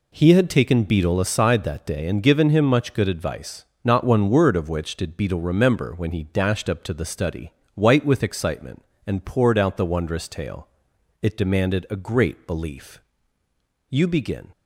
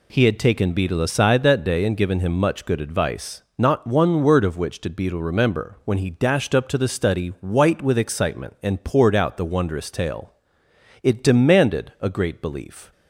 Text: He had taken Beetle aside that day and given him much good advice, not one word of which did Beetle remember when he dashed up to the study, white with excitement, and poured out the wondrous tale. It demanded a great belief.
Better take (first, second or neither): second